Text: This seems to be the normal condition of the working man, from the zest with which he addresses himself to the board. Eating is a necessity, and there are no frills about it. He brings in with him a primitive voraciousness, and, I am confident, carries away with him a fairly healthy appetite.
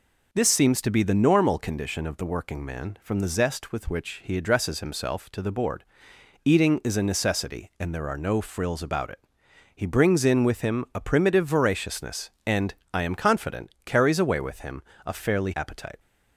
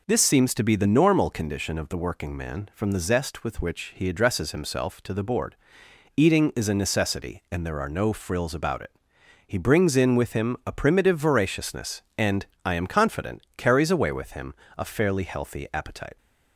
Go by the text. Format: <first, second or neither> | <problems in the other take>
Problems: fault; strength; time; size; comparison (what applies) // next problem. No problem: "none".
second | pauses between "him" and "a"; slight; at 14.8 s; 0.22 s long; slight in the second // skips "healthy"; at 15.5 s